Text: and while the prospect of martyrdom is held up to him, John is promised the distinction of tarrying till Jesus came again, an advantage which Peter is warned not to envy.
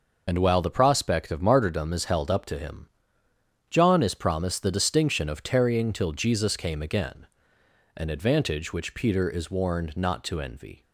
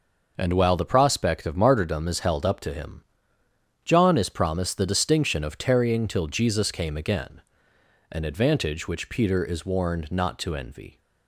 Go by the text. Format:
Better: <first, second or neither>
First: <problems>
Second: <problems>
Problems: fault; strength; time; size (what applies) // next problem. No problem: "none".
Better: second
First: loses the start of "and"; at 0.2 s; 55 ms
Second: none